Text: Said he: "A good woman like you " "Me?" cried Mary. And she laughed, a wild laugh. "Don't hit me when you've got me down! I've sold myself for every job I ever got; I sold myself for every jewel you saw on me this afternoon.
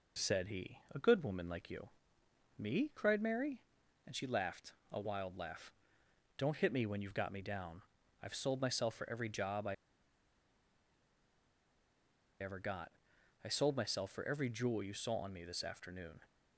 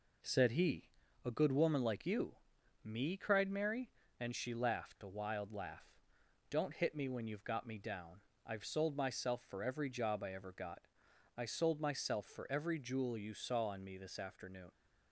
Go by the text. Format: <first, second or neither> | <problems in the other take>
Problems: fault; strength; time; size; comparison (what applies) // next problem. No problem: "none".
second | pauses between "I" and "ever"; strong; at 9.7 s; 2.6 s long